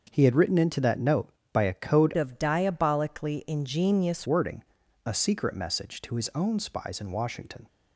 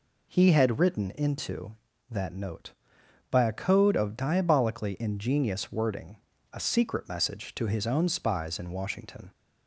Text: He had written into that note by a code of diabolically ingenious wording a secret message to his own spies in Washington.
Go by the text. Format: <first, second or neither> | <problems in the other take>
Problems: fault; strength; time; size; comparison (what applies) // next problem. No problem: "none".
second | starts louder than the rest; noticeable; until 1.1 s; 6 dB // changes voice from "of" to "ingenious"; from 2.1 to 4.2 s; 2.1 s long // pauses between "wording" and "a"; at 4.6 s; 0.42 s long; slight in the second